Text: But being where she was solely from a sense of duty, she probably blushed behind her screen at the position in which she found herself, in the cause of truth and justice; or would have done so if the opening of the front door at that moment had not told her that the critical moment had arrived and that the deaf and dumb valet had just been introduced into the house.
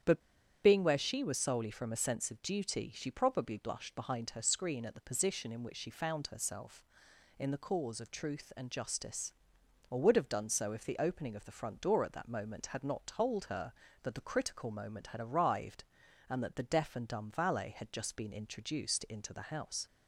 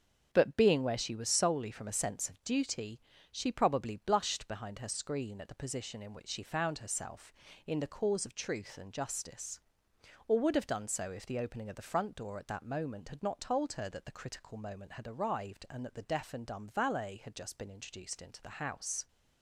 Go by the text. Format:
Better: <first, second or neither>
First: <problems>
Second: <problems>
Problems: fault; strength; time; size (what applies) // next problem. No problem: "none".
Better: second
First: starts louder than the rest; strong; until 1.4 s; 8.5 dB // pauses between "But" and "being"; at 0.2 s; 0.44 s long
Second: starts louder than the rest; strong; until 1.3 s; 7.5 dB